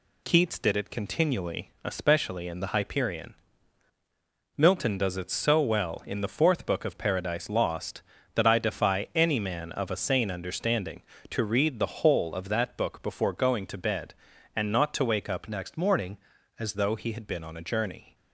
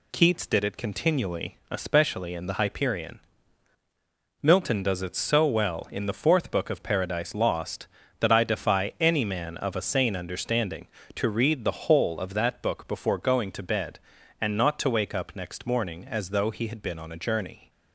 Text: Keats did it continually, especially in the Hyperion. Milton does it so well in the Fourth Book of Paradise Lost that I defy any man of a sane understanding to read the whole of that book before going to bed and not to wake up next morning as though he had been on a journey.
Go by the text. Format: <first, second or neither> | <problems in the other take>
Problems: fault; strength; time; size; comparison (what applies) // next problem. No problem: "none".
second | changes voice from "next" to "as"; from 15.4 to 16.7 s; 1.3 s long